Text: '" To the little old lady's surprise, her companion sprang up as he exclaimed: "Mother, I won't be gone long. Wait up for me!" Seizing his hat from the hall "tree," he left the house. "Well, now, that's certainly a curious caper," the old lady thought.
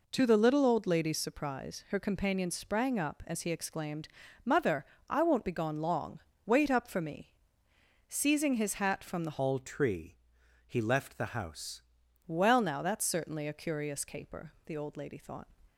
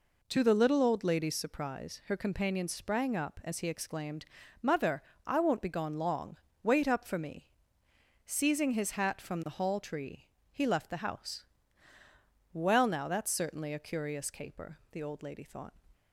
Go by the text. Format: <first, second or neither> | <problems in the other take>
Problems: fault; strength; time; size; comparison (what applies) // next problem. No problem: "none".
second | changes voice from "hall" to "house"; from 9.3 to 11.8 s; 2.5 s long